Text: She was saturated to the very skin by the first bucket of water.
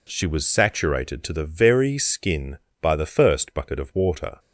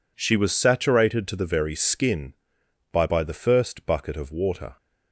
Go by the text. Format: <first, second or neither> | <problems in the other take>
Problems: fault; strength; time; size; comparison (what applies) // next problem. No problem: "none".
first | says "by" twice; at 3.0 s